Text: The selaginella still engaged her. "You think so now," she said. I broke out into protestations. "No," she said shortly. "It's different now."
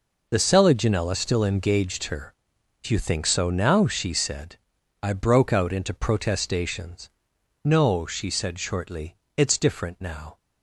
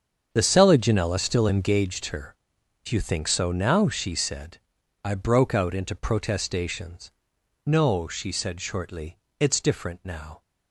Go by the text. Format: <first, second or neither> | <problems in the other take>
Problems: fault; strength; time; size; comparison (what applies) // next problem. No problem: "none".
first | starts louder than the rest; strong; until 1.9 s; 7.5 dB